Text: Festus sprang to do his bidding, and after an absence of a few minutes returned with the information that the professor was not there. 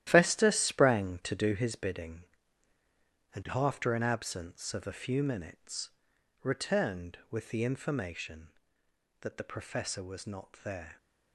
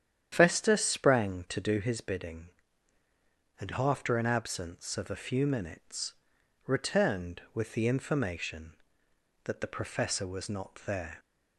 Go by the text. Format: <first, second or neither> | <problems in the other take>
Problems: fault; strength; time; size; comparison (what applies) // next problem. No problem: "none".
second | gets quieter; strong; throughout; 10.5 dB // starts louder than the rest; strong; until 1.1 s; 12.5 dB; strong in the second // pauses between "minutes" and "returned"; noticeable; at 5.8 s; 0.52 s long; noticeable in the second